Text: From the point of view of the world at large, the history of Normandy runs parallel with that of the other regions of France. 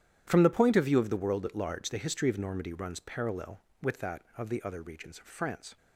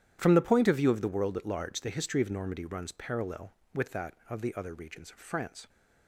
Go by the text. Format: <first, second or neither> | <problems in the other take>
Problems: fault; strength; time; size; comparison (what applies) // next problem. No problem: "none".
neither | starts louder than the rest; strong; the same in both